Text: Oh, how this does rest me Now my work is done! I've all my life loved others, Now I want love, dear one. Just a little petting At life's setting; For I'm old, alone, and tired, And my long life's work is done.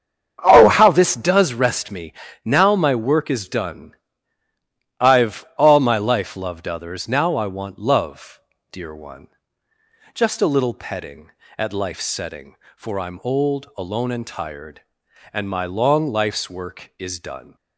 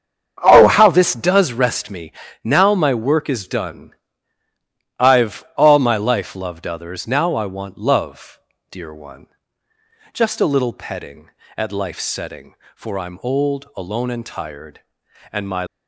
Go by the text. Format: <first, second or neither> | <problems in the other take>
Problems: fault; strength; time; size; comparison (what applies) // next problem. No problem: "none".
first | starts louder than the rest; strong; until 1.4 s; 8 dB; strong in the first // pauses between "me" and "Now"; slight; at 2.1 s; 0.32 s long; slight in the first // stops before "long life's work is done"; at 15.6 s